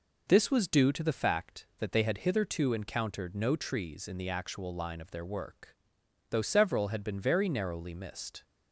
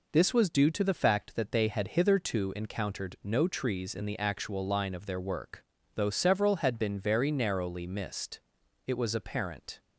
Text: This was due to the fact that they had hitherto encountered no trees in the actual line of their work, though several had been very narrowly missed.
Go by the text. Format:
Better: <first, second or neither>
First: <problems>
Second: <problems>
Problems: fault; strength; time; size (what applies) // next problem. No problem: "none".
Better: first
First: none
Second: goes on to say "It was apparent"; noticeable; from 8.8 s on; 0.94 s long